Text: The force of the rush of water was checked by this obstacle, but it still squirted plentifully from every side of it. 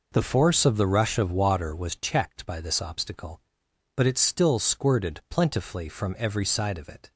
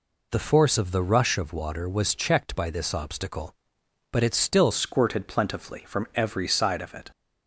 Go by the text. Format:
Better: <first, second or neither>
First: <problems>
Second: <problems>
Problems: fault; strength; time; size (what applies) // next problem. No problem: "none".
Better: first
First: none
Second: changes voice at "squirted"; from 4.7 s on; 2.4 s long